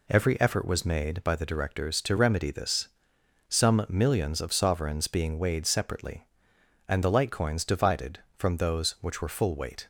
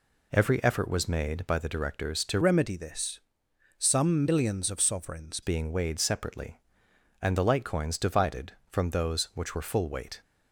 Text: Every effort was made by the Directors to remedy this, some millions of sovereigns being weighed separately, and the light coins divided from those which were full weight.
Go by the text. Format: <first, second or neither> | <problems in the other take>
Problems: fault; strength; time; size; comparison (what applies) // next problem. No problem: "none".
first | changes voice from "remedy" to "sovereigns"; from 2.4 to 5.4 s; 3.0 s long